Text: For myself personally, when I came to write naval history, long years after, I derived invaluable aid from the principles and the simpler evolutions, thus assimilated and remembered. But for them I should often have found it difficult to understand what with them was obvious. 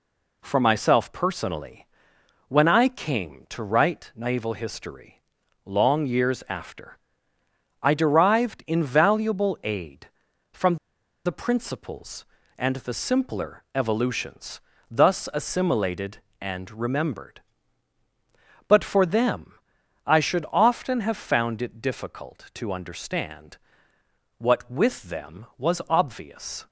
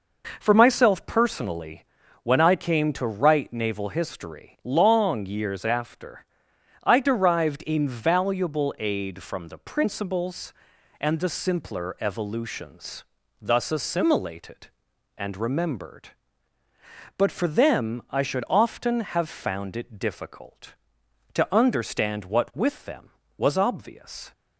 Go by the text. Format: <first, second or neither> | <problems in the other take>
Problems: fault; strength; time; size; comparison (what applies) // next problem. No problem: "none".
second | pauses between "from" and "the"; noticeable; at 10.7 s; 0.50 s long // pauses between "them" and "I"; noticeable; at 19.5 s; 0.52 s long // pauses between "understand" and "what"; noticeable; at 23.5 s; 0.80 s long